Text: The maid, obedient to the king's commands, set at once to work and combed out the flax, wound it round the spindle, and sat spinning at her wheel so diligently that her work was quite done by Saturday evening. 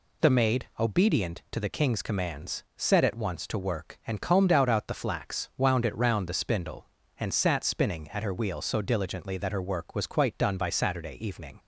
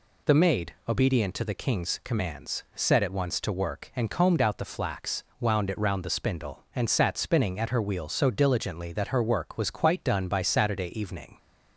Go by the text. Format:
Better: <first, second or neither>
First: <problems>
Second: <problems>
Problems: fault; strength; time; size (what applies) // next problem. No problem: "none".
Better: second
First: says "out" twice; at 4.6 s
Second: none